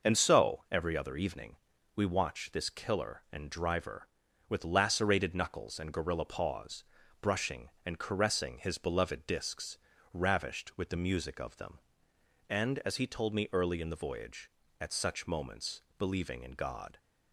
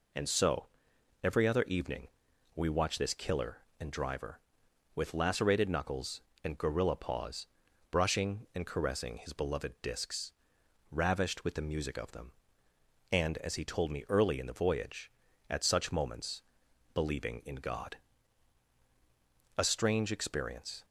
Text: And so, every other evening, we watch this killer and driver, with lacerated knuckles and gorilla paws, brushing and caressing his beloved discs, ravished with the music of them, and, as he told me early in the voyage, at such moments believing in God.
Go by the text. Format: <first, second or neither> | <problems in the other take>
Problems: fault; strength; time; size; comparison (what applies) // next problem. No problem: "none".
first | pauses between "moments" and "believing"; noticeable; at 16.4 s; 0.50 s long; slight in the first // goes on to say "A strange experience"; noticeable; from 19.5 s on; 1.2 s long